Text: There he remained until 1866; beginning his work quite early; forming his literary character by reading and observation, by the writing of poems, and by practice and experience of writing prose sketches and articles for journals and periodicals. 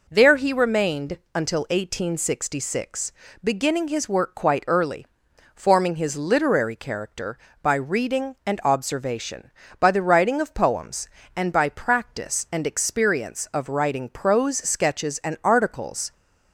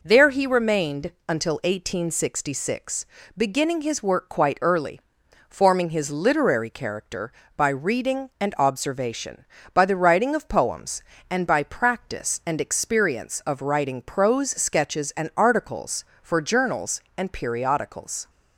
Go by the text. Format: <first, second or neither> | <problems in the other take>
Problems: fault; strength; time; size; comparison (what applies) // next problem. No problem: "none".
second | pauses between "remained" and "until"; slight; at 1.1 s; 0.18 s long; slight in the second // stops before "for journals and periodicals"; at 16.1 s